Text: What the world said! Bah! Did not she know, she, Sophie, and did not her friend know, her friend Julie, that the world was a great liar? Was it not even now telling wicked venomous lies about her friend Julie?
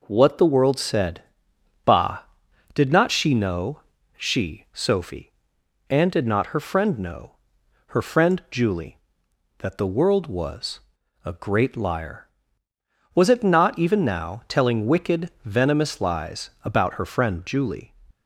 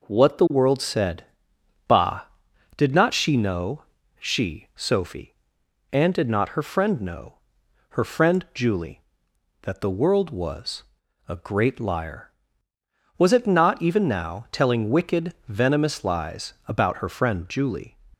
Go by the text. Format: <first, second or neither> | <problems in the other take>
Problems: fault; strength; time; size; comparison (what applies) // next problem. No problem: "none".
neither | pauses between "was" and "a"; the same in both